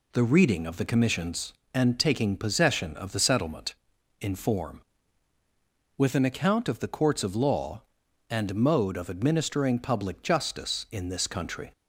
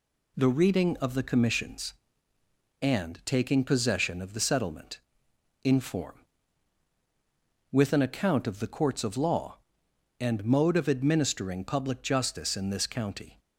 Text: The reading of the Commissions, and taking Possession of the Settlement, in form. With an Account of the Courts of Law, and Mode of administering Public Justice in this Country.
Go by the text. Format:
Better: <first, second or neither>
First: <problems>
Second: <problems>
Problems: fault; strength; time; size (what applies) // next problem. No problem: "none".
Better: first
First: none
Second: says "County" for "Country"; at 12.8 s